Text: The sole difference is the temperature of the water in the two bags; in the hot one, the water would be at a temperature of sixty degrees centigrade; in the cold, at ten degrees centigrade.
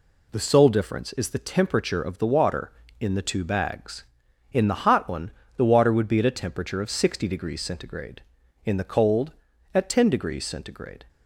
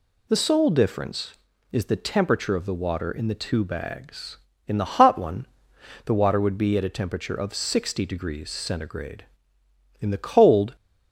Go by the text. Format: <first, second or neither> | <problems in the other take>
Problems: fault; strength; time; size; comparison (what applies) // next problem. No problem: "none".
first | stops before "at ten degrees centigrade"; at 10.7 s